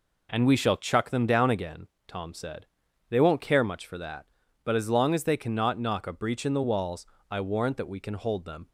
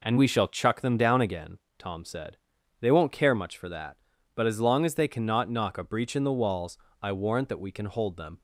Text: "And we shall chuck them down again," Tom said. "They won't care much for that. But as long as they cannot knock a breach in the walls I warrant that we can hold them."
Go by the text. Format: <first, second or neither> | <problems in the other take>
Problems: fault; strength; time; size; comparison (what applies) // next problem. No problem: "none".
neither | pauses between "walls" and "I"; slight; the same in both